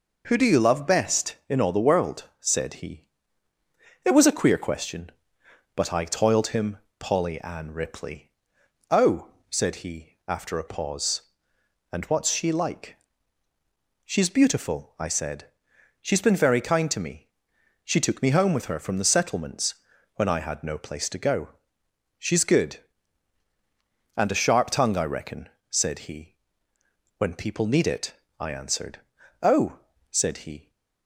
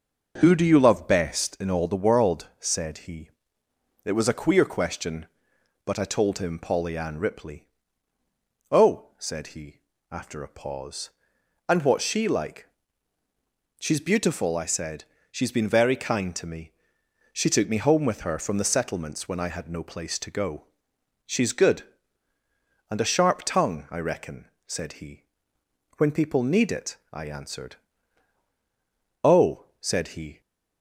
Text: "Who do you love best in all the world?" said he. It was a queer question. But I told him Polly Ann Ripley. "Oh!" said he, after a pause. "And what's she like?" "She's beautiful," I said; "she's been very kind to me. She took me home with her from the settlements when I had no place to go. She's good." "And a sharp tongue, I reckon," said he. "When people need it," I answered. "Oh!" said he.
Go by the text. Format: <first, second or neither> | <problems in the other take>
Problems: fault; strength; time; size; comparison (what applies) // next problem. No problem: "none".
second | says "toiled" for "told"; at 6.0 s // pauses between "him" and "Polly"; slight; at 6.7 s; 0.20 s long // pauses between "settlements" and "when"; at 19.7 s; 0.42 s long